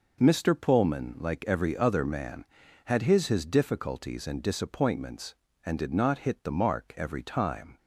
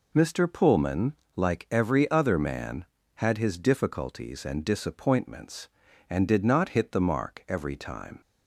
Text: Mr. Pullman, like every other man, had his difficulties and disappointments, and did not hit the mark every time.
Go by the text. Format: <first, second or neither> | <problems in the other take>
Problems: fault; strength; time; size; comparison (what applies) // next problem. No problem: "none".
second | says "his" twice; at 3.2 s